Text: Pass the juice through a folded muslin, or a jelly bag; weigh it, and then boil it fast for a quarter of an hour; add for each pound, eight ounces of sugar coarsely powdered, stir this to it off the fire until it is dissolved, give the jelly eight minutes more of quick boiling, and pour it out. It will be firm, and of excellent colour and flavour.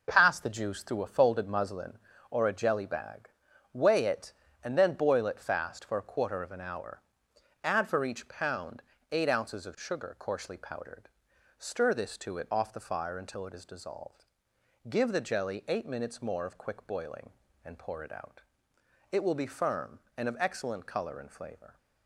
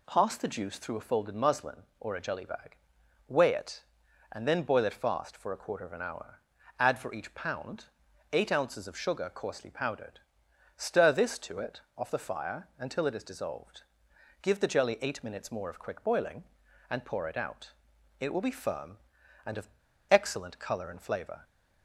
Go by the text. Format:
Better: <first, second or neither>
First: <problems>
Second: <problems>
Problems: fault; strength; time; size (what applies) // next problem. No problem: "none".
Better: first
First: none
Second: pauses between "it" and "off"; slight; at 11.8 s; 0.16 s long // pauses between "of" and "excellent"; at 19.7 s; 0.39 s long